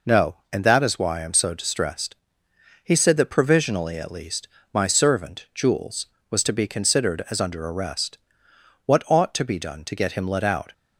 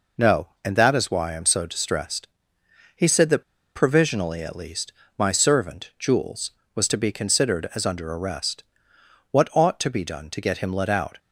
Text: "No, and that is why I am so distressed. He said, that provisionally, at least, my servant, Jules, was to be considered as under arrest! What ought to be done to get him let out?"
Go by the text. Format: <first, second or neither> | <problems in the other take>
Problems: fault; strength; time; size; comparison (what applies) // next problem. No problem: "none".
first | pauses between "that" and "provisionally"; slight; at 3.4 s; 0.32 s long